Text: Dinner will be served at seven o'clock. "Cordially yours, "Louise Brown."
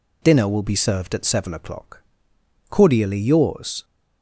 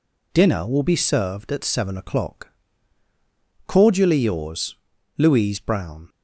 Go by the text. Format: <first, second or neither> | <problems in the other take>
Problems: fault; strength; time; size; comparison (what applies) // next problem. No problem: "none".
second | stops before "Louise Brown"; at 3.8 s